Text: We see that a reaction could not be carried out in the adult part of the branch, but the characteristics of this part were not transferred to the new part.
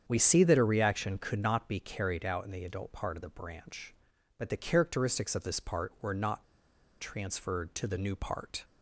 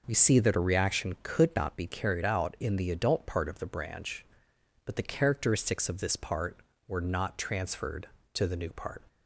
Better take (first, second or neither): second